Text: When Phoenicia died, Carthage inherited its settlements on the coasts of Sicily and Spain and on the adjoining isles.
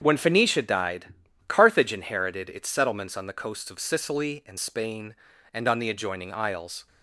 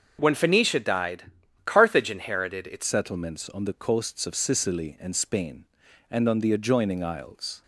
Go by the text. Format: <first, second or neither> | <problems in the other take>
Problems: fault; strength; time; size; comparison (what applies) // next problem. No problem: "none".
first | starts louder than the rest; until 1.2 s; 6.5 dB; strong in the first // changes voice at "settlements"; from 2.8 s on; 4.8 s long